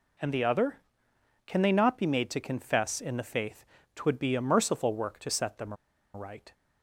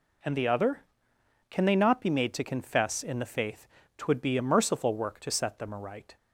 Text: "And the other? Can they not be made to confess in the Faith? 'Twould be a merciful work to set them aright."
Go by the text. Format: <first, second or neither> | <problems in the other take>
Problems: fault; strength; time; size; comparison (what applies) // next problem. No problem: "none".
second | pauses between "them" and "aright"; at 5.7 s; 0.40 s long